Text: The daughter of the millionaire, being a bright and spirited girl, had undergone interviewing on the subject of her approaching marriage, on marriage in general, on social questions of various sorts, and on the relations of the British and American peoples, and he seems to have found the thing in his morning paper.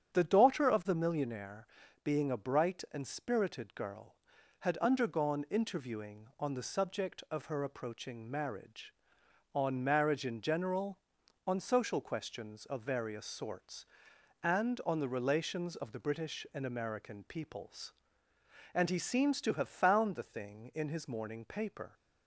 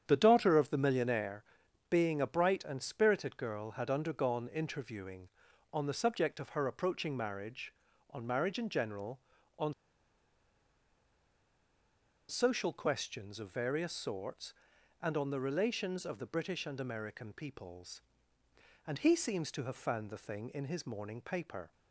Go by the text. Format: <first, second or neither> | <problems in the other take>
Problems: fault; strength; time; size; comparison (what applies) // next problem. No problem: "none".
first | starts louder than the rest; strong; until 1.0 s; 9 dB; strong in the first // pauses between "on" and "social"; strong; at 9.7 s; 2.5 s long